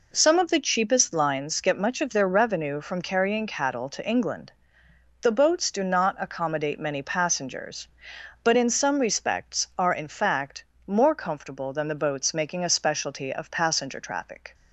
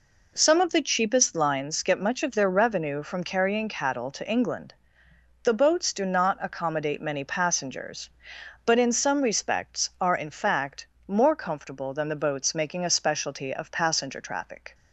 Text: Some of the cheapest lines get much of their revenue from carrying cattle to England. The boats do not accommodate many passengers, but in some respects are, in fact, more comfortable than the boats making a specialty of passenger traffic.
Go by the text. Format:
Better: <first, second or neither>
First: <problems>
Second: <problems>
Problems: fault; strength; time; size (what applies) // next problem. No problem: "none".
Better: neither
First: none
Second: none